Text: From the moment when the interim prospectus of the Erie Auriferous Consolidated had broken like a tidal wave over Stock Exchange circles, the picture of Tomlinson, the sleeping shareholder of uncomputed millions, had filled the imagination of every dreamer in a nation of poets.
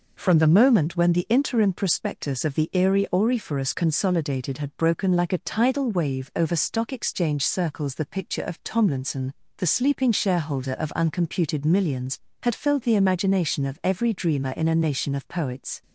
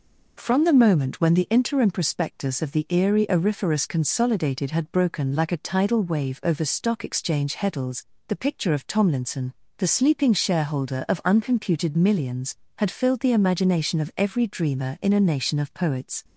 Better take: first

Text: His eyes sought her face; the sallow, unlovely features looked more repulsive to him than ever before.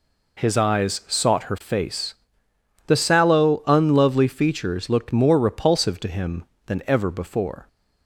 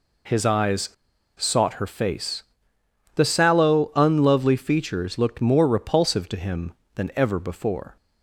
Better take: first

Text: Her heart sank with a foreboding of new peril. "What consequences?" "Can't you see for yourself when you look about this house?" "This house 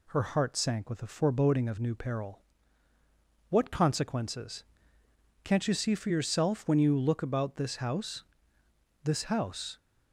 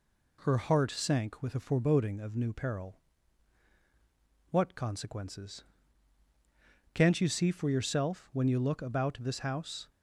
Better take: first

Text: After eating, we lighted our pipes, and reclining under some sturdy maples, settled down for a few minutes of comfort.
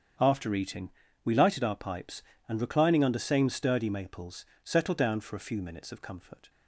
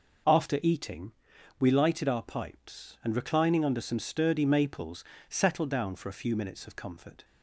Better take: second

